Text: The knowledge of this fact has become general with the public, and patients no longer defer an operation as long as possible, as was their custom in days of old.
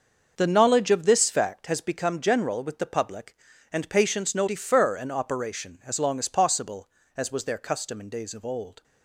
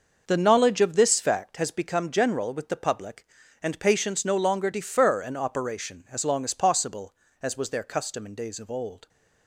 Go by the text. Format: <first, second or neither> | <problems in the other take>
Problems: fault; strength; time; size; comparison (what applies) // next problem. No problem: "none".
second | starts louder than the rest; until 1.3 s; 6.5 dB; noticeable in the second // skips "longer"; at 4.4 s